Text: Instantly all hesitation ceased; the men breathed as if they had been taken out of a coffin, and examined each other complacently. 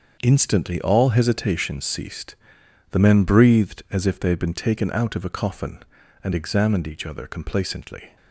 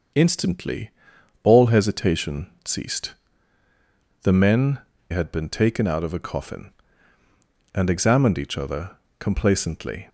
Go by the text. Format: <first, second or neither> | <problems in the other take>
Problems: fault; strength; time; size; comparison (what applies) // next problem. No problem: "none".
first | starts louder than the rest; until 1.6 s; 6.5 dB; also in the first // pauses between "Instantly" and "all"; noticeable; at 0.9 s; 0.52 s long // pauses between "hesitation" and "ceased"; slight; at 2.4 s; 0.16 s long // skips "breathed as if they"; at 4.9 s // pauses between "other" and "complacently"; slight; at 8.9 s; 0.22 s long